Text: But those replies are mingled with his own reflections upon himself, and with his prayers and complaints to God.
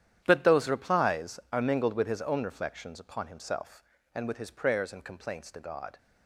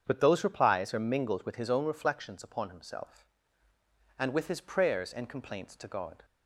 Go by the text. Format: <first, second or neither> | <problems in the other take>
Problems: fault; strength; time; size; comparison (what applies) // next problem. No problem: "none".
second | gets quieter; strong; throughout; 14 dB // starts louder than the rest; strong; until 1.2 s; 10 dB; strong in the second